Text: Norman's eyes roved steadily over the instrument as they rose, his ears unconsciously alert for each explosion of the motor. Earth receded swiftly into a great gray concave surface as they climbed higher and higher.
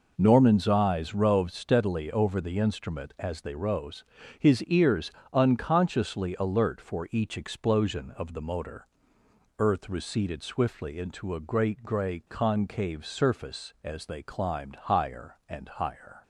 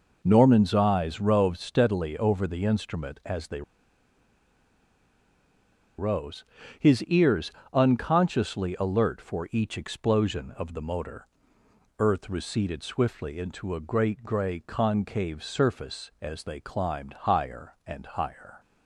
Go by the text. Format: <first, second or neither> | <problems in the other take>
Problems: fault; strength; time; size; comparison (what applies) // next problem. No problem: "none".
first | pauses between "they" and "rose"; strong; at 3.6 s; 2.3 s long // pauses between "ears" and "unconsciously"; slight; at 7.4 s; 0.22 s long; slight in the first